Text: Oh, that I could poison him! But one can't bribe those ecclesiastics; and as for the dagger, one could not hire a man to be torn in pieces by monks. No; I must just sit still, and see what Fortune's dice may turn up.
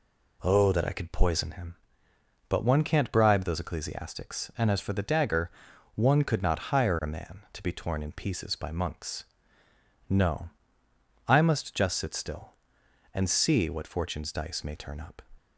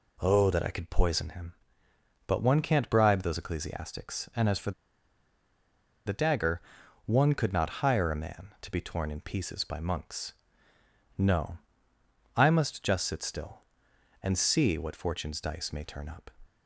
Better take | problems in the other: first | pauses between "for" and "the"; strong; at 4.7 s; 1.3 s long

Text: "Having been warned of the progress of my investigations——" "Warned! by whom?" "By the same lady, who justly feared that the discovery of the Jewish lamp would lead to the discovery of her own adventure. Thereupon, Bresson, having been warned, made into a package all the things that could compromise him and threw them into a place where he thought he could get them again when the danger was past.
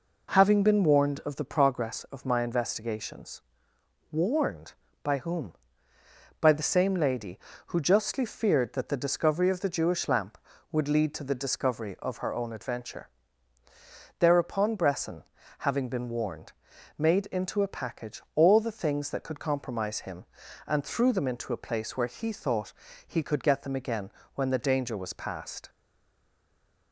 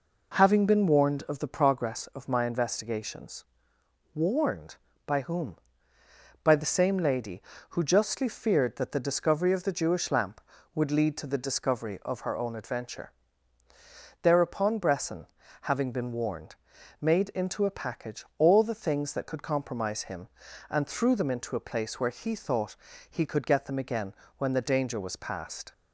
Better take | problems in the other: second | pauses between "thought" and "he"; slight; at 22.7 s; 0.36 s long; slight in the second // pauses between "again" and "when"; slight; at 24.1 s; 0.24 s long; slight in the second // stays silent after the last word; noticeable; from 25.6 s on; 1.3 s long

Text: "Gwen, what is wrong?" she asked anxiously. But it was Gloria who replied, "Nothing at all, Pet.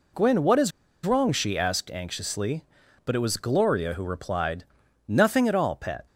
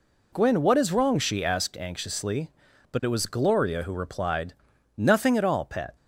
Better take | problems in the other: second | pauses between "is" and "wrong"; slight; at 0.7 s; 0.34 s long

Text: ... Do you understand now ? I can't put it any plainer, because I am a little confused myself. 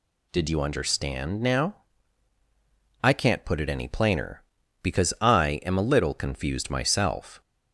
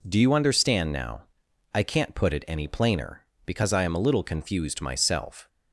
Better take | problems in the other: second | says "Did" for "Do"; at 0.3 s

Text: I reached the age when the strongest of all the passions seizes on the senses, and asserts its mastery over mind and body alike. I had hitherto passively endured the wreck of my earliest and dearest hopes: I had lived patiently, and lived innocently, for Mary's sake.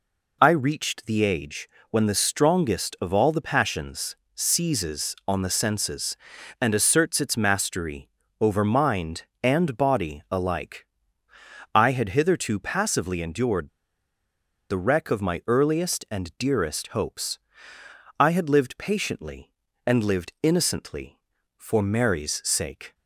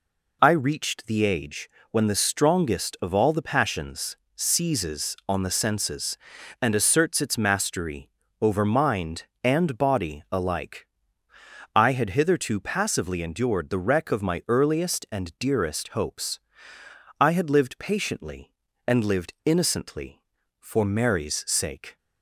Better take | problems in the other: second | pauses between "age" and "when"; slight; at 1.6 s; 0.22 s long; slight in the second // pauses between "passions" and "seizes"; slight; at 4.1 s; 0.22 s long; slight in the second // pauses between "mastery" and "over"; slight; at 8.0 s; 0.32 s long; slight in the second // pauses between "endured" and "the"; at 13.6 s; 1.0 s long

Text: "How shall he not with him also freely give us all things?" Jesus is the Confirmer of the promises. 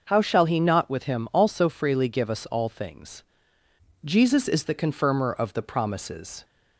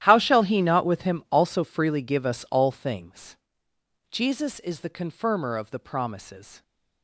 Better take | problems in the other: first | gets quieter; strong; throughout; 18 dB

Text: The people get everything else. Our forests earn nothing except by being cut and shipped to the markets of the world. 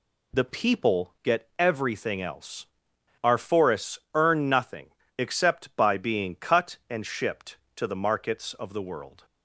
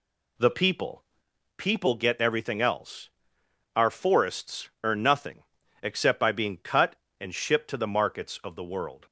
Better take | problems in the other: first | says "people" twice; at 1.5 s // pauses between "forests" and "earn"; slight; at 4.6 s; 0.16 s long; slight in the first // pauses between "nothing" and "except"; at 5.4 s; 0.38 s long; slight in the first

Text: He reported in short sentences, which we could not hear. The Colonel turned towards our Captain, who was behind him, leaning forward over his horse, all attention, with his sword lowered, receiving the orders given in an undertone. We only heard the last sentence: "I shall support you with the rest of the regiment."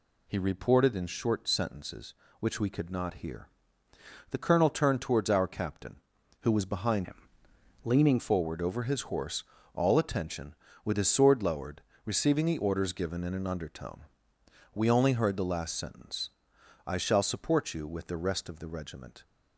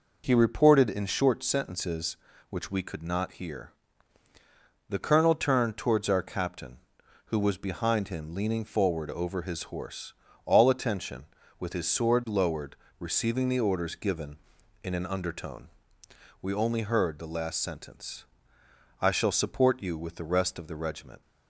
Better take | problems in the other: second | changes voice from "him" to "leaning"; from 7.0 to 8.1 s; 1.1 s long

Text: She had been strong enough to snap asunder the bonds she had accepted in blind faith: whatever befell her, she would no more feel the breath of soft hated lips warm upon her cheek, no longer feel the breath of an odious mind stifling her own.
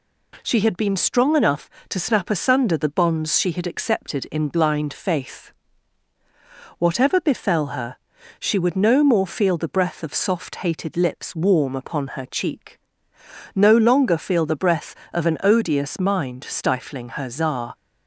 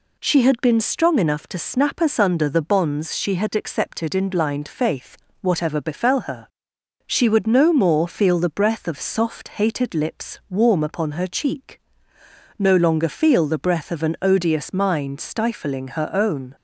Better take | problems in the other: second | says "czar" for "own"; at 17.2 s

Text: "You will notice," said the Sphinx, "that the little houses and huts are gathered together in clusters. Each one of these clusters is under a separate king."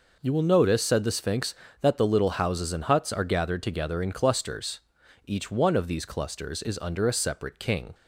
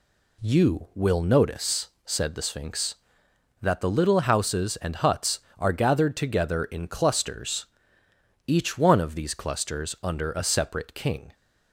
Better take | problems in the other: first | skips "is"; at 9.9 s

